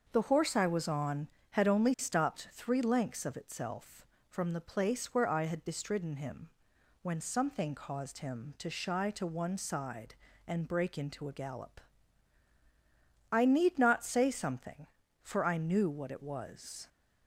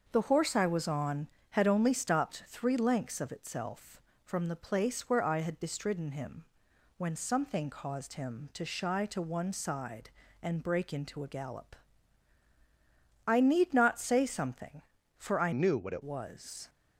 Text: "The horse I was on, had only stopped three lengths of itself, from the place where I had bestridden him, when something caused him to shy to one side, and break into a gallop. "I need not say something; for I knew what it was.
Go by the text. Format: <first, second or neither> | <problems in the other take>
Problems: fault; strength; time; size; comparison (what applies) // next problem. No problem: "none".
first | starts louder than the rest; until 1.1 s; 6 dB; also in the first // changes voice from "knew" to "it"; from 15.5 to 16.0 s; 0.5 s long